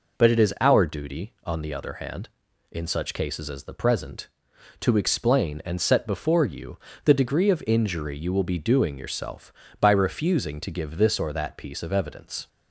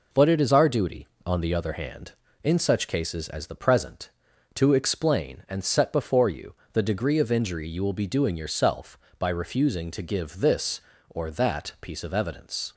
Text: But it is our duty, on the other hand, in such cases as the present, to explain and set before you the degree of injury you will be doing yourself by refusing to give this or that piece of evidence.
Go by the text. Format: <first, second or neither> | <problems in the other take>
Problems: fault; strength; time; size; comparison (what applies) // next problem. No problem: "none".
neither | pauses between "you" and "the"; slight; the same in both